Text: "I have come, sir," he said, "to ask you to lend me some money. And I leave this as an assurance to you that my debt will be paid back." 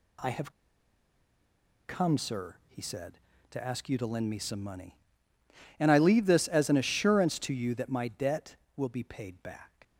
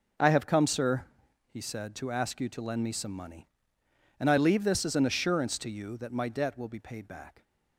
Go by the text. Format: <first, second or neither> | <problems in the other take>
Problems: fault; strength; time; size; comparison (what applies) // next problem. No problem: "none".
second | pauses between "have" and "come"; strong; at 0.5 s; 1.3 s long